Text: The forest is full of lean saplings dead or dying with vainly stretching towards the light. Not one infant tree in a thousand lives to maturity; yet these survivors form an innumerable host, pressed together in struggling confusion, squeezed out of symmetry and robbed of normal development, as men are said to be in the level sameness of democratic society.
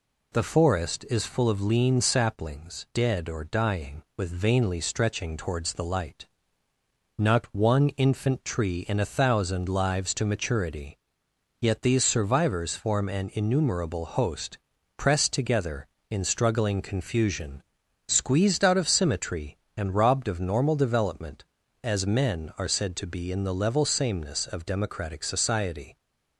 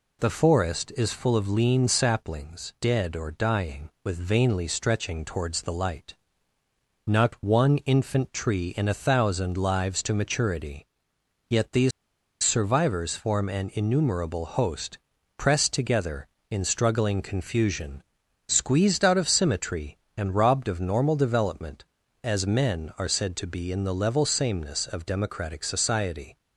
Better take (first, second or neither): first